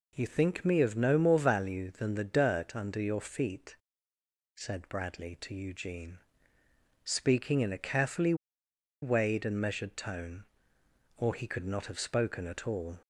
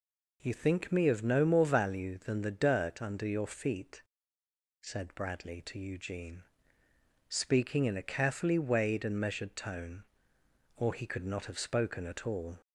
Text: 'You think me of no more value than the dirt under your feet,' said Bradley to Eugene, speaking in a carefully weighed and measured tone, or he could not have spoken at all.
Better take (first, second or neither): second